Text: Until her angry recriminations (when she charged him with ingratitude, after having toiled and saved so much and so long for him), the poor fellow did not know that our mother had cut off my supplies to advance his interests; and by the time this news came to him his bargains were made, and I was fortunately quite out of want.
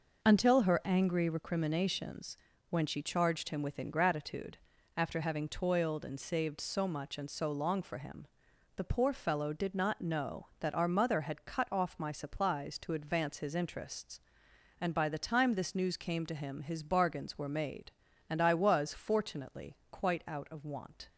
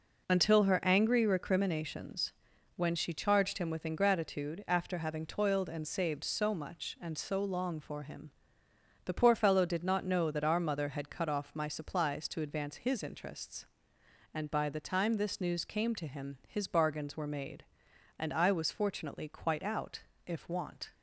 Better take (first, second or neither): first